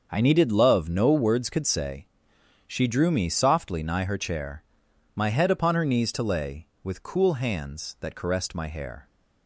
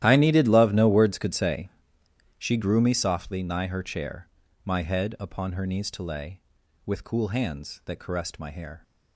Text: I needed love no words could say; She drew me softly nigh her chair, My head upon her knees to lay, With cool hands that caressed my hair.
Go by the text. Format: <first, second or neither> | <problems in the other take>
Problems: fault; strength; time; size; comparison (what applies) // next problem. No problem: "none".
first | starts louder than the rest; strong; until 1.0 s; 13 dB; also in the first // says "grew" for "drew"; at 2.5 s